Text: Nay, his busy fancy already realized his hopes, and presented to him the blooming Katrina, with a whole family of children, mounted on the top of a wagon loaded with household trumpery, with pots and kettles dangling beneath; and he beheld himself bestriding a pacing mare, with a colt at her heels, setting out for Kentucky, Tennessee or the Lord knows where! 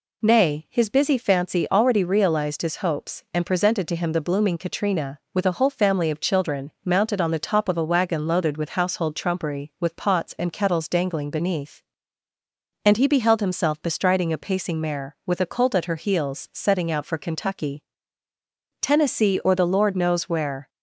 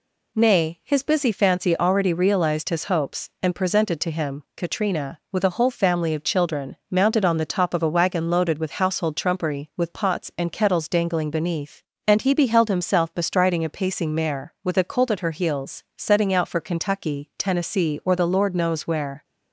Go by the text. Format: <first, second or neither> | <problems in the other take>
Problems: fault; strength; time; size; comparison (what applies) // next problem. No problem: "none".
first | skips "the blooming"; at 4.4 s